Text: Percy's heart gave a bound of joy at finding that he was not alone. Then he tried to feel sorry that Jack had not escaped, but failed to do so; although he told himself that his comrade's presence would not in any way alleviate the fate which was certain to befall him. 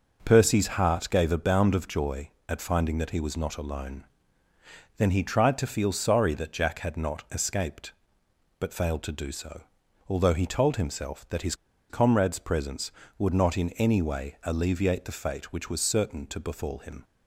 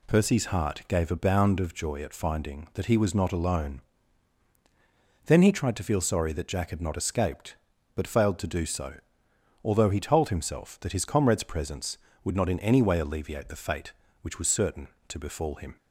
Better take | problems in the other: second | pauses between "his" and "comrade's"; slight; at 11.5 s; 0.34 s long

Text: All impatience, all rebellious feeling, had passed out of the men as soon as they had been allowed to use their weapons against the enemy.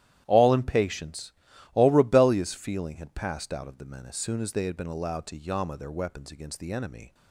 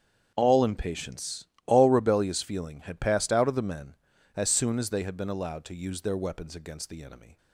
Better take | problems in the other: second | starts louder than the rest; strong; until 1.2 s; 12.5 dB; strong in the second // says "yama" for "use"; at 5.3 s

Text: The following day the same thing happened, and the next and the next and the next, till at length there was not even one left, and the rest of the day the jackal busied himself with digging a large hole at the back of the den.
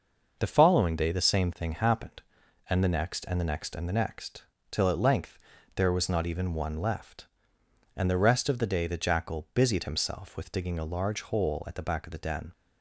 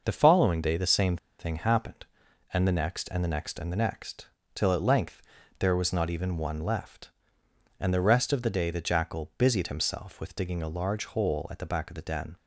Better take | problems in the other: first | pauses between "same" and "thing"; slight; at 1.1 s; 0.21 s long // pauses between "length" and "there"; at 5.2 s; 0.38 s long; also in the first

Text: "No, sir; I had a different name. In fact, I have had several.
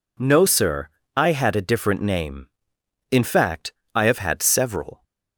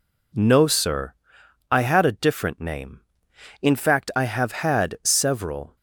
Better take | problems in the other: neither | none

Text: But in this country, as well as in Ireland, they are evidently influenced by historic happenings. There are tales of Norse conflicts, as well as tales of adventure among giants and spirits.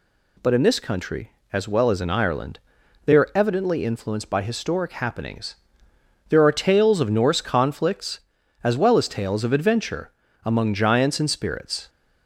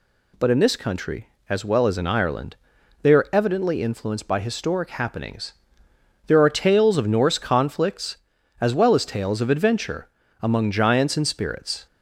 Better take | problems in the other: neither | pauses between "adventure" and "among"; slight; the same in both

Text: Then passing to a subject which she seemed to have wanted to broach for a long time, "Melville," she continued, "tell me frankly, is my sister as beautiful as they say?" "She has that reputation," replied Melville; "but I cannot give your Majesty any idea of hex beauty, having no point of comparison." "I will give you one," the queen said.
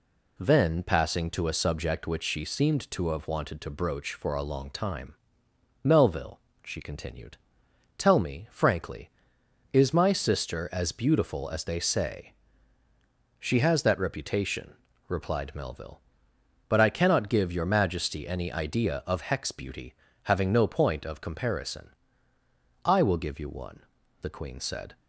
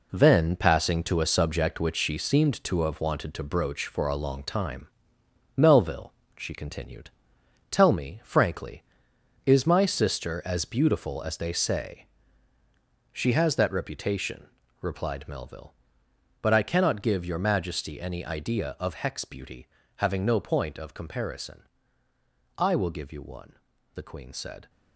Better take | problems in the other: first | gets quieter; strong; throughout; 8.5 dB

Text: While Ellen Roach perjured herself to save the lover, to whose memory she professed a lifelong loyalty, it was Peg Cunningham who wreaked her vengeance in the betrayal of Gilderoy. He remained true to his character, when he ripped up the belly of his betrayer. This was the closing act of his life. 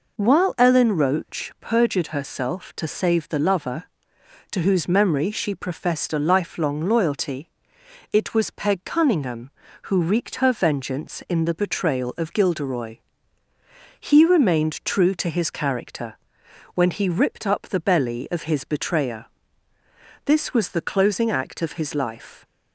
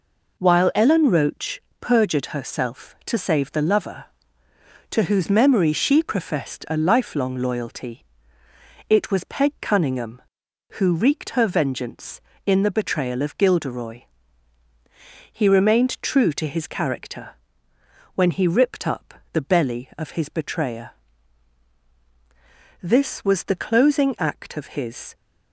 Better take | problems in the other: first | pauses between "Roach" and "perjured"; slight; at 1.6 s; 0.18 s long // pauses between "up" and "the"; slight; at 19.1 s; 0.18 s long // stops before "life"; at 25.1 s

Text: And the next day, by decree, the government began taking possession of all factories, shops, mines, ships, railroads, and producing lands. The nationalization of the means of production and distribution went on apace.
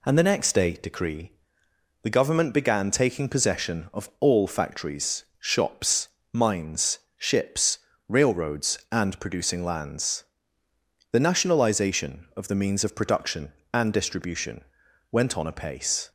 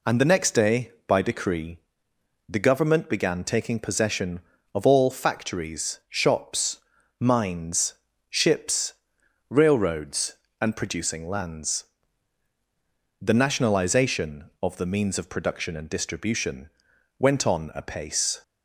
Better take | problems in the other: second | skips "by"; at 0.7 s // pauses between "distribution" and "went"; noticeable; at 14.6 s; 0.48 s long; noticeable in the second

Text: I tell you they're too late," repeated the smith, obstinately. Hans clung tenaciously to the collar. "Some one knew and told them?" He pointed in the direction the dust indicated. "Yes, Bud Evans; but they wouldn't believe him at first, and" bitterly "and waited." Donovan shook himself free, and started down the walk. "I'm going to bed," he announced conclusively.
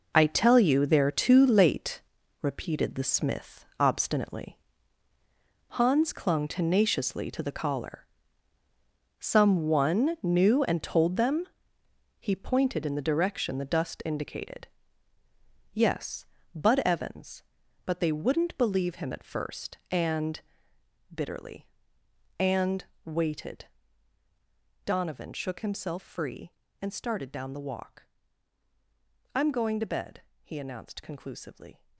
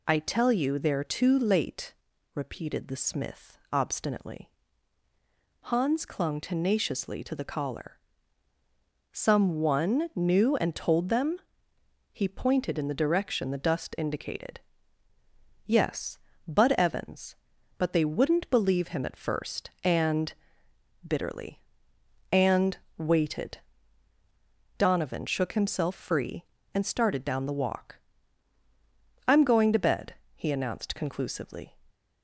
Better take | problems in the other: second | gets quieter; strong; throughout; 11 dB // pauses between "and" and "bitterly"; noticeable; at 20.4 s; 0.72 s long; noticeable in the second // pauses between "and" and "waited"; slight; at 22.8 s; 0.20 s long; slight in the second

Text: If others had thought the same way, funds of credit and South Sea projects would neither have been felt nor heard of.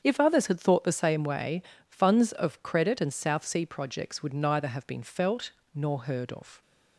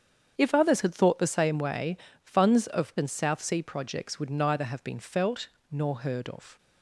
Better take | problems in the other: first | starts louder than the rest; strong; until 1.3 s; 7.5 dB; strong in the first // skips "credit"; at 2.9 s // pauses between "felt" and "nor"; slight; at 5.4 s; 0.22 s long; slight in the first

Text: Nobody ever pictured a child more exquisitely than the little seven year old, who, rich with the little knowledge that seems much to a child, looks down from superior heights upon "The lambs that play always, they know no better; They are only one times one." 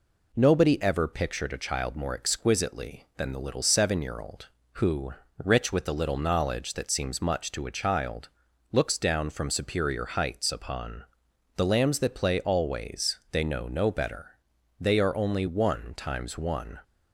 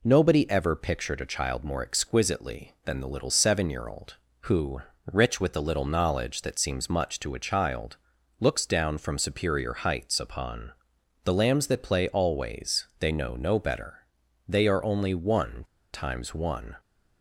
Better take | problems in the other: first | pauses between "upon" and "The"; noticeable; at 10.7 s; 0.52 s long; noticeable in the first // pauses between "one" and "times"; slight; at 15.6 s; 0.27 s long

